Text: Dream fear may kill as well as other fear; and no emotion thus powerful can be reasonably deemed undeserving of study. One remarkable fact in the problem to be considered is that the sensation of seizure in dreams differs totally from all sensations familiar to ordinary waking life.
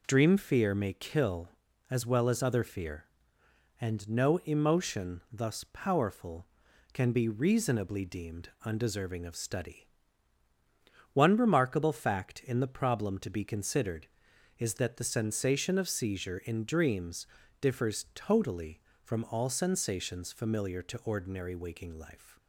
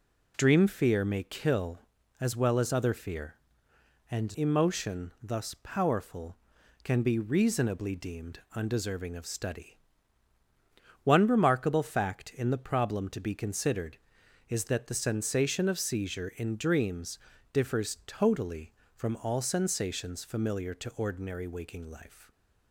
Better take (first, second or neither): first